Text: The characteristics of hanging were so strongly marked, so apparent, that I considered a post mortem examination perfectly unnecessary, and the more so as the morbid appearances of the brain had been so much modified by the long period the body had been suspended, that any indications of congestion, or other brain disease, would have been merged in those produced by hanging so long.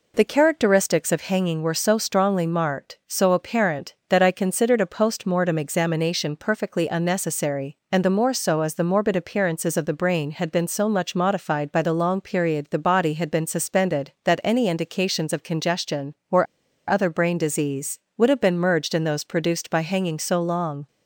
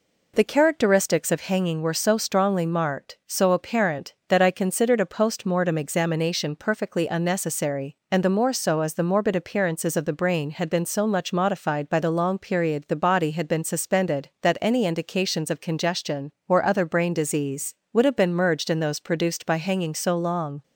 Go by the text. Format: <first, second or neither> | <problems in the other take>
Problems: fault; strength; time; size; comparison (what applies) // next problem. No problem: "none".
second | pauses between "or" and "other"; at 16.4 s; 0.43 s long